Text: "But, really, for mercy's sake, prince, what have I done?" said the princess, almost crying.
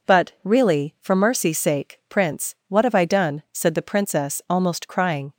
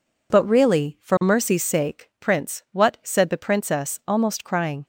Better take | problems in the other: first | skips "have I done"; at 2.9 s

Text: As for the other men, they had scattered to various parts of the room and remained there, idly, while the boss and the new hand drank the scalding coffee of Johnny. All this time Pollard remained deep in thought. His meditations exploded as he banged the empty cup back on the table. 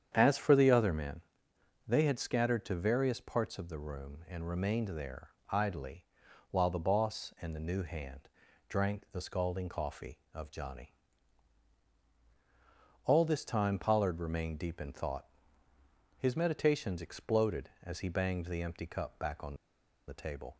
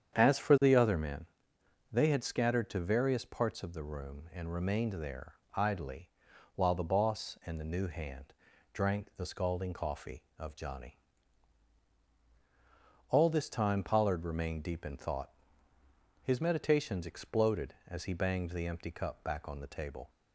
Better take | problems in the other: second | starts louder than the rest; strong; until 1.1 s; 8.5 dB; strong in the second // pauses between "hand" and "drank"; at 8.2 s; 0.40 s long; also in the second // pauses between "on" and "the"; noticeable; at 19.5 s; 0.52 s long

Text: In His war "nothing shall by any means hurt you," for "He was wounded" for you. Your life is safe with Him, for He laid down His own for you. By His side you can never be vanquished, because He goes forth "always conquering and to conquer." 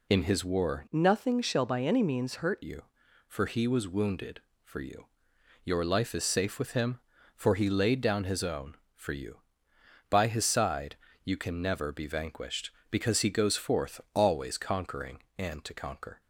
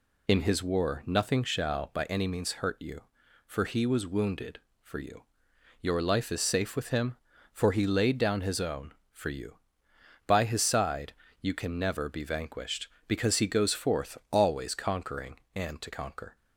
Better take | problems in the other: second | changes voice from "nothing" to "hurt"; from 0.9 to 2.6 s; 1.7 s long // pauses between "side" and "you"; slight; at 10.9 s; 0.28 s long; slight in the second

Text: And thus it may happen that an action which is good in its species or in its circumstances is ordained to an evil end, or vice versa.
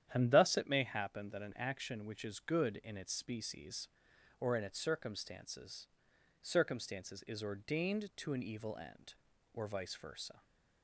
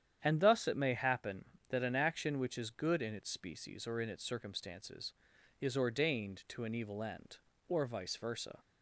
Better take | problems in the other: second | starts louder than the rest; strong; until 1.1 s; 10 dB; strong in the second // says "circumstances" twice; at 6.4 s

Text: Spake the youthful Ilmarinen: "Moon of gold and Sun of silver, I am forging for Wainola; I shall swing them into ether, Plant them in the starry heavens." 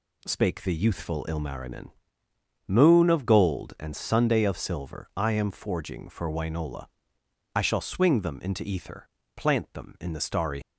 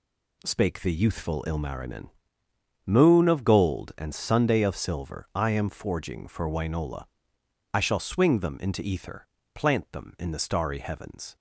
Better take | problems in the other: second | stops before "heavens"; at 10.6 s

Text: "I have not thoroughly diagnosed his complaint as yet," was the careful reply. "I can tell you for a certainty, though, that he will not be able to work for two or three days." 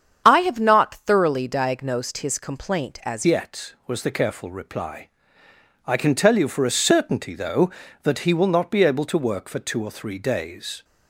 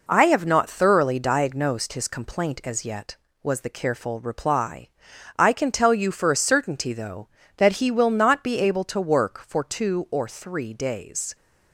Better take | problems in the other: second | starts louder than the rest; strong; until 1.2 s; 7.5 dB // changes voice at "yet"; from 3.2 s on; 7.6 s long

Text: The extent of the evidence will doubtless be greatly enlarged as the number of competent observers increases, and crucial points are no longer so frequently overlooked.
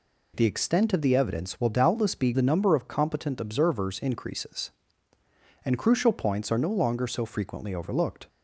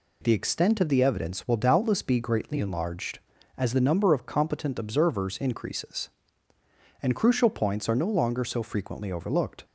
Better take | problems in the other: second | skips "greatly enlarged as"; at 2.3 s

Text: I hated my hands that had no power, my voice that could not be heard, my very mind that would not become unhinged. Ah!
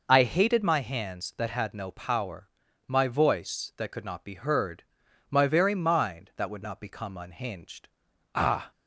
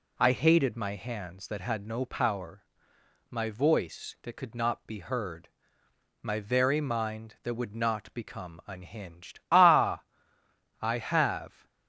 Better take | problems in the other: first | goes on to say "I have"; noticeable; from 10.8 s on; 0.86 s long

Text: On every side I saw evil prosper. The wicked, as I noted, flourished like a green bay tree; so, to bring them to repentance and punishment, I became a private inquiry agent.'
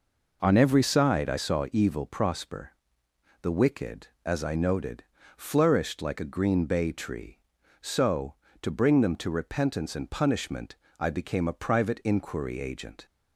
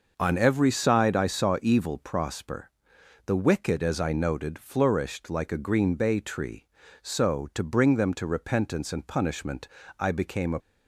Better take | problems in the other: first | stops before "private inquiry agent"; at 10.5 s

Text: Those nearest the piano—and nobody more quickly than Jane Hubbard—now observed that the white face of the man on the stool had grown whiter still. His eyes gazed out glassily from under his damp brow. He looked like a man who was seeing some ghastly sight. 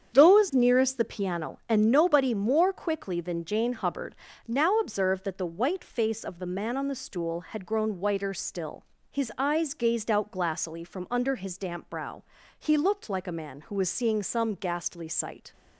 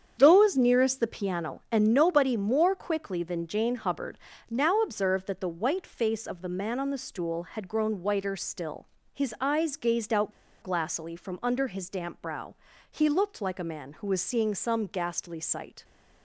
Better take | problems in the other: first | starts louder than the rest; strong; until 1.1 s; 8 dB; strong in the first // pauses between "out" and "glassily"; slight; at 10.3 s; 0.31 s long

